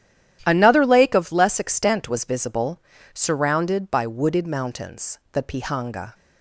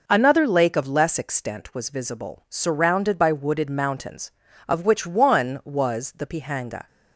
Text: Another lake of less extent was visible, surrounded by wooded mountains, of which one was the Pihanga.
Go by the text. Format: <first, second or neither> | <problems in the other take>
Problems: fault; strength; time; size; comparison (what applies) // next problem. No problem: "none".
second | starts louder than the rest; strong; until 1.4 s; 11.5 dB // skips "of which one was"; at 5.2 s